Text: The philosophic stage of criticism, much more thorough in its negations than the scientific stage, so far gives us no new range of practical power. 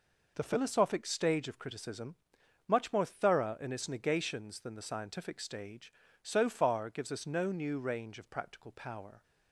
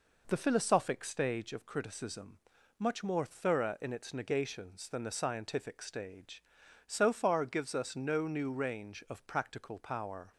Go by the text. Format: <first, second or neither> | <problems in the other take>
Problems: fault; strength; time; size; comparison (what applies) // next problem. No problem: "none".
neither | none